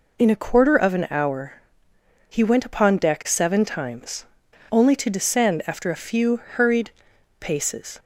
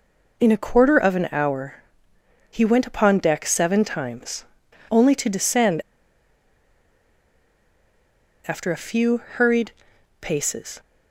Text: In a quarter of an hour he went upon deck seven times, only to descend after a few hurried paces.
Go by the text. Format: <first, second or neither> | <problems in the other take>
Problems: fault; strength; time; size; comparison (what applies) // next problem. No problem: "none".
first | pauses between "hour" and "he"; noticeable; at 1.7 s; 0.74 s long; noticeable in the first // pauses between "descend" and "after"; strong; at 5.8 s; 2.6 s long // pauses between "hurried" and "paces"; noticeable; at 9.6 s; 0.50 s long; noticeable in the first